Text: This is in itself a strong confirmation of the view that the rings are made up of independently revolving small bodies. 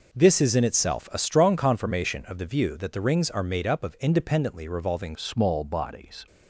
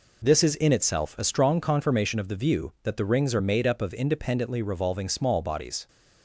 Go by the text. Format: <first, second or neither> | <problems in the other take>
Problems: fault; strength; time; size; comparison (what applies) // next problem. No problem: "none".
second | changes voice at "small"; from 5.1 s on; 1.1 s long